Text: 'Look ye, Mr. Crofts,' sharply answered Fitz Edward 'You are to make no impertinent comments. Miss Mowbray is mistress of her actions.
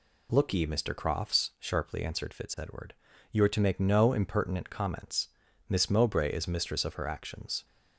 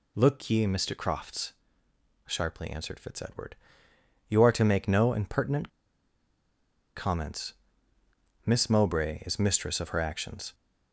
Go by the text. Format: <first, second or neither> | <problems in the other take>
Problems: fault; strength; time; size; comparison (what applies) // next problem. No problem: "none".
first | pauses between "Edward" and "You"; noticeable; at 3.5 s; 0.74 s long; slight in the first // pauses between "impertinent" and "comments"; strong; at 5.6 s; 1.2 s long